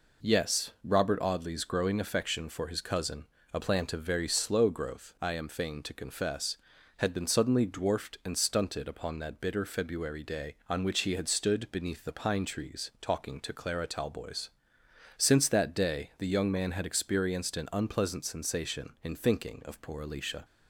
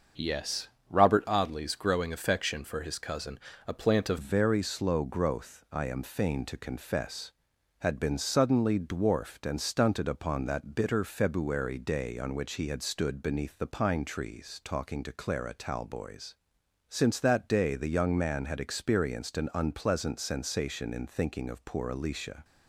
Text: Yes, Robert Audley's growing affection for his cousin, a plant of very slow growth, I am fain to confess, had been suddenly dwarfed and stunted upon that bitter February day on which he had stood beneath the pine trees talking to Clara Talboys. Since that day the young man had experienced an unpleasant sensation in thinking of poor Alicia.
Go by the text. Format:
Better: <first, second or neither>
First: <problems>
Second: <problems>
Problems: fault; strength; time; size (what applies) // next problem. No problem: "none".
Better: first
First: none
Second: starts louder than the rest; until 1.4 s; 6.5 dB // changes voice at "very"; from 4.2 s on; 18.2 s long